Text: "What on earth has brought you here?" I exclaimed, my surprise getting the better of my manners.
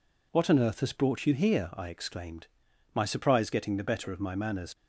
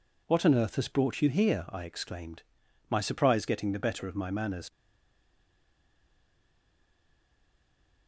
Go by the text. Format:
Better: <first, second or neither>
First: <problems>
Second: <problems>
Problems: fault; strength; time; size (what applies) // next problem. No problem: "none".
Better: first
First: none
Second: stays silent after the last word; strong; from 4.7 s on; 3.3 s long